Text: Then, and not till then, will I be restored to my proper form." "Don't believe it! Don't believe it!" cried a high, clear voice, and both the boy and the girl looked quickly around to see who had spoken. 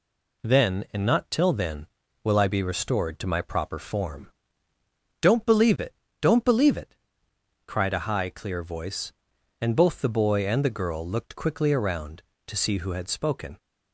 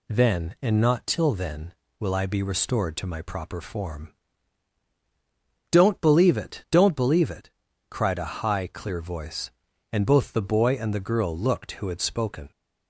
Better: first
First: none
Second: skips "quickly around to see"; at 11.7 s

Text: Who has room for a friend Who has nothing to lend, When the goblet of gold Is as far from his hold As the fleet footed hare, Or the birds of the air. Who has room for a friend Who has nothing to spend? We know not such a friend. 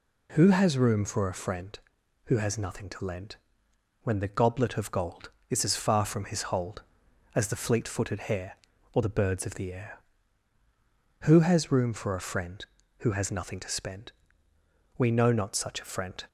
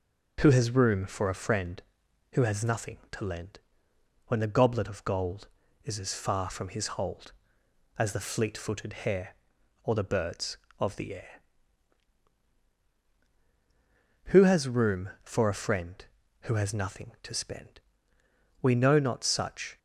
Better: first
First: none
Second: stops before "a friend"; at 19.7 s

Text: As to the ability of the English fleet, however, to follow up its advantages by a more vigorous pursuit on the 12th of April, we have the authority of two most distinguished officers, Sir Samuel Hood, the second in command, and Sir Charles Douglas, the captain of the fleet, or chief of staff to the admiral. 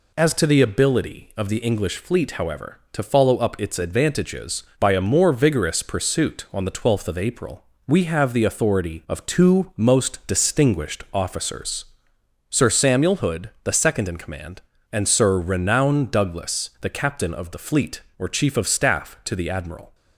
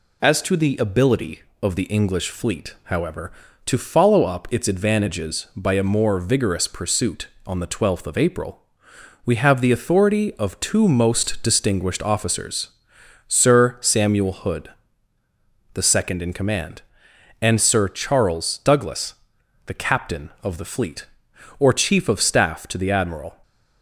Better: second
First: says "Renown" for "Charles"; at 15.3 s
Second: none

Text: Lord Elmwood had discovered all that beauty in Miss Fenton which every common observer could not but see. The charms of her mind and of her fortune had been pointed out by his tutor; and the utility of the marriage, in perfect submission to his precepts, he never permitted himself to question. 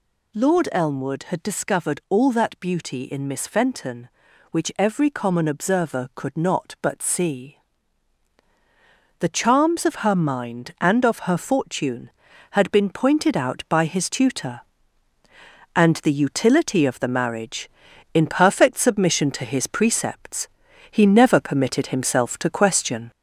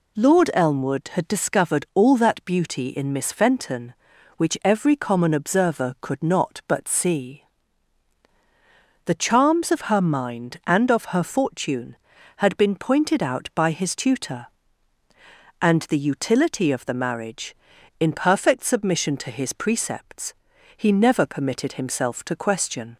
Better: second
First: gets louder; slight; throughout; 3 dB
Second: none

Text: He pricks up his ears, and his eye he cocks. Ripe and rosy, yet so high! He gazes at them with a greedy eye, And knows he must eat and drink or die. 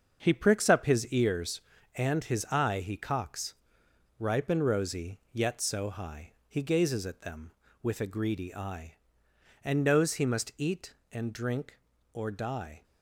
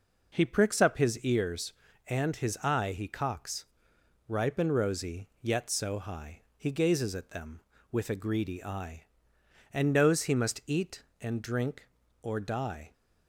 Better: second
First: gets quieter; strong; throughout; 7.5 dB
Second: none

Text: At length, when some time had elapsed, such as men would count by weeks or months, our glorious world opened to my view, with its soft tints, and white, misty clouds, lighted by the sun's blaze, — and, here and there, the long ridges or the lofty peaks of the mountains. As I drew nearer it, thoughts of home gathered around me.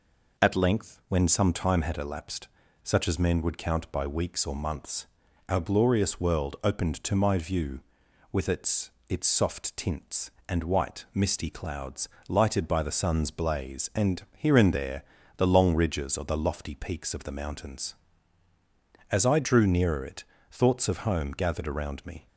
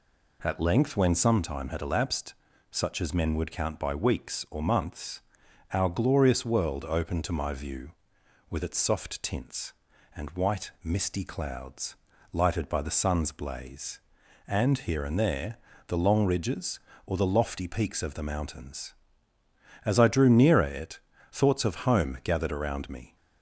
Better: second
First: says "its" twice; at 9.0 s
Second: none

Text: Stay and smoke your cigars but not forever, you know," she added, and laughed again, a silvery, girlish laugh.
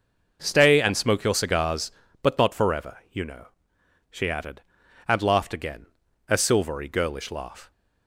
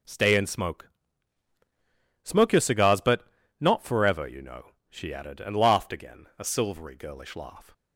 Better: first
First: none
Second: says "smoke" twice; at 2.2 s // pauses between "but" and "not"; slight; at 3.2 s; 0.32 s long

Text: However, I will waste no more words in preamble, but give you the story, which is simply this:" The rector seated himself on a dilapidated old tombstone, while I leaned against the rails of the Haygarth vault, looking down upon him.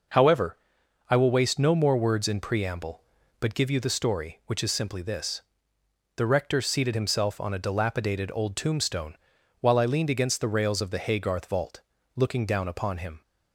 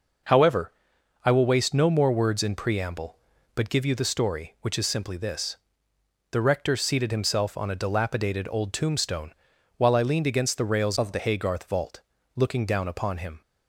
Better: first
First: none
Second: changes voice from "of" to "the"; from 10.9 to 11.1 s; 0.2 s long

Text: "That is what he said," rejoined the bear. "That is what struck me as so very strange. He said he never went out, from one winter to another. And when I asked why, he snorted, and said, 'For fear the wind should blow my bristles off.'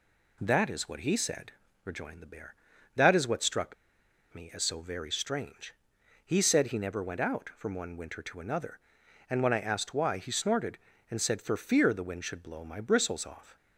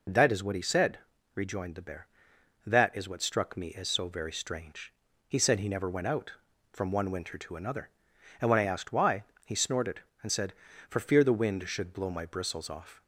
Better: second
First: pauses between "struck" and "me"; noticeable; at 3.7 s; 0.59 s long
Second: none

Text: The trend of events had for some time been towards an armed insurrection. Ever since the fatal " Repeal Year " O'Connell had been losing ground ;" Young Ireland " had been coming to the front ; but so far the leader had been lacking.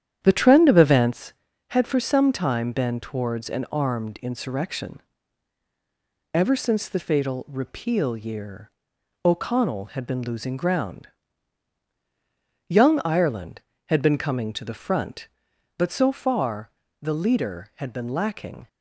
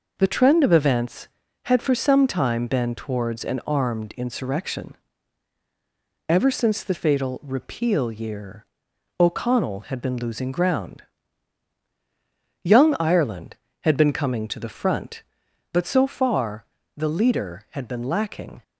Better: second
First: starts louder than the rest; strong; until 1.2 s; 10 dB // pauses between "far" and "the"; slight; at 16.6 s; 0.32 s long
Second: pauses between "far" and "the"; slight; at 16.6 s; 0.32 s long

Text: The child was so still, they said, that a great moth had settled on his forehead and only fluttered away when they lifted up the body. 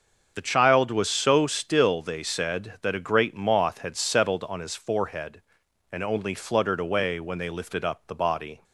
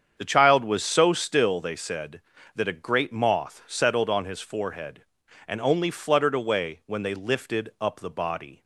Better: first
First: starts louder than the rest; until 1.3 s; 6.5 dB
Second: starts louder than the rest; strong; until 1.1 s; 7.5 dB // skips "had"; at 3.6 s

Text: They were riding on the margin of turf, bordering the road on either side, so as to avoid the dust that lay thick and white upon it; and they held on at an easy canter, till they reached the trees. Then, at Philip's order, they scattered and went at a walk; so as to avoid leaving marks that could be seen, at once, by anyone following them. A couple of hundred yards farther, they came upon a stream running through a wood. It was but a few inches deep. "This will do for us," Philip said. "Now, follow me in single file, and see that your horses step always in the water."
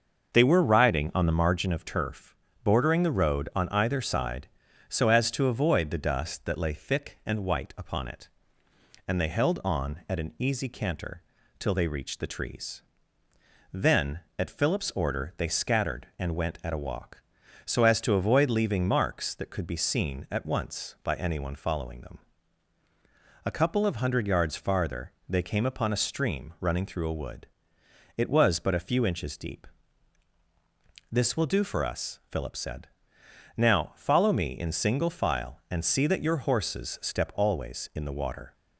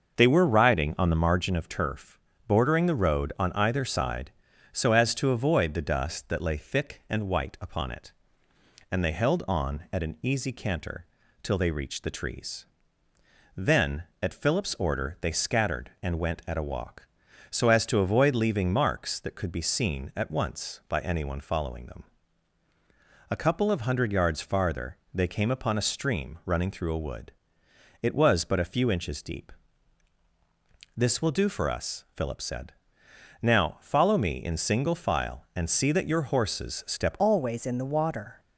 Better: first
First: starts louder than the rest; until 1.3 s; 6 dB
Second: starts louder than the rest; until 1.2 s; 6 dB // changes voice at "always"; from 37.1 s on; 1.2 s long

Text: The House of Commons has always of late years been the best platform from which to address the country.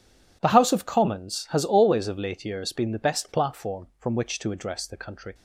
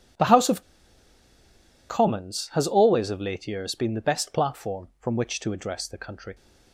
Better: first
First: none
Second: pauses between "of" and "Commons"; strong; at 0.6 s; 1.2 s long

